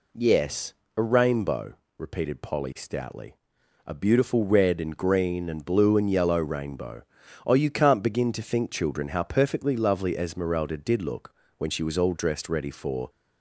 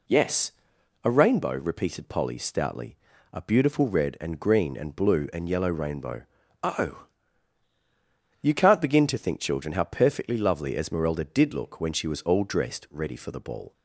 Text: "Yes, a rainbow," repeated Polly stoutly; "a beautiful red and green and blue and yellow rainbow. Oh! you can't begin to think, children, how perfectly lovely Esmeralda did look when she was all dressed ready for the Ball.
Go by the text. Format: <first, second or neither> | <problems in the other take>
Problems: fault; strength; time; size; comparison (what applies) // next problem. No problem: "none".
second | pauses between "look" and "when"; slight; at 11.3 s; 0.24 s long // stops before "the Ball"; at 13.0 s